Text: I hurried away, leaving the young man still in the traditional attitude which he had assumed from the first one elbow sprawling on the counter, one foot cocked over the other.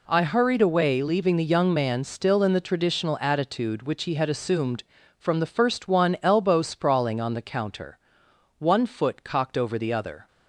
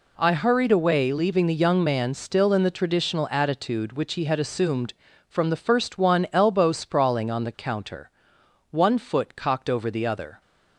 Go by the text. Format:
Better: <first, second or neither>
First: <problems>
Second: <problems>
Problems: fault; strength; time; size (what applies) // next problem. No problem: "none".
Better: neither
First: none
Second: none